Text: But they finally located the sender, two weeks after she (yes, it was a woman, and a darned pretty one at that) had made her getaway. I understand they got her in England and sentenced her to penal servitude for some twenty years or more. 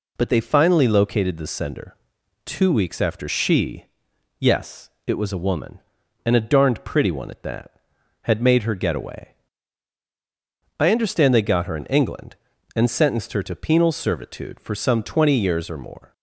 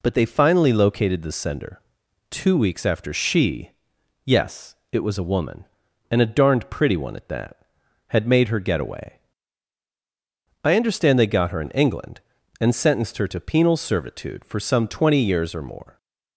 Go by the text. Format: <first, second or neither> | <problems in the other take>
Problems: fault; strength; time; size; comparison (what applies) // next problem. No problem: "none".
neither | none